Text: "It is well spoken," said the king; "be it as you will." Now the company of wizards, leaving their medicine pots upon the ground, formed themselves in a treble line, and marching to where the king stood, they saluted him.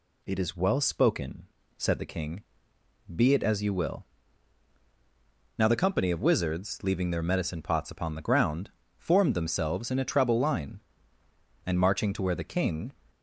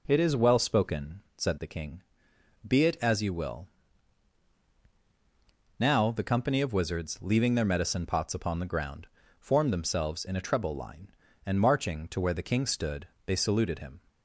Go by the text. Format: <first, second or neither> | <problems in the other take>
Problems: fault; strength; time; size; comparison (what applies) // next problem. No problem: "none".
second | stops before "stood they saluted him"; at 13.1 s